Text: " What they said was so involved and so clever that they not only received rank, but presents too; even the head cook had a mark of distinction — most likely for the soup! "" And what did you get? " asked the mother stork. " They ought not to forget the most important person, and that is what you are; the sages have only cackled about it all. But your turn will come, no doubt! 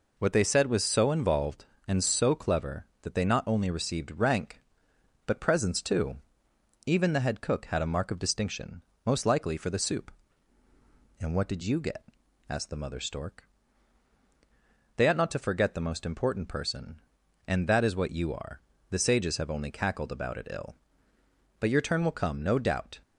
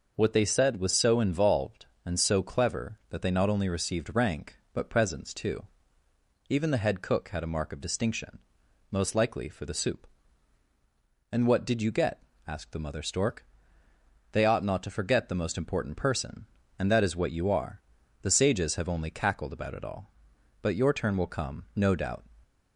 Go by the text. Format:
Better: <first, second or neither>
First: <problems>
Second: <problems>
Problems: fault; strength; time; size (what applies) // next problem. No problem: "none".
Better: second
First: says "ill" for "all"; at 20.4 s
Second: none